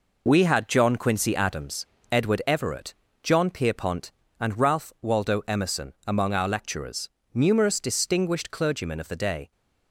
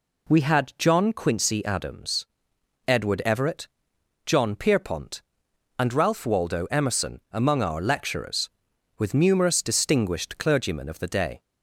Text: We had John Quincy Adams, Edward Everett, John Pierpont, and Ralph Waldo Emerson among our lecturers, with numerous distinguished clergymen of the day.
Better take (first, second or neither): second